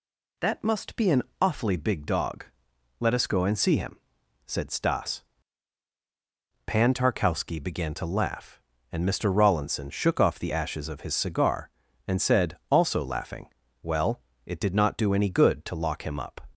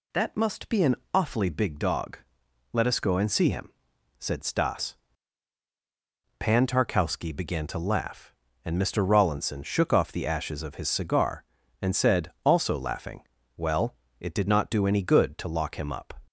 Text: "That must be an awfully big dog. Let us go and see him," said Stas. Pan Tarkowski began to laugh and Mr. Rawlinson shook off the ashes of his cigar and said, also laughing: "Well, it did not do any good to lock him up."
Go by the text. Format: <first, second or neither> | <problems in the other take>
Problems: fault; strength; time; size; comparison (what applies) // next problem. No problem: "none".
neither | pauses between "an" and "awfully"; slight; the same in both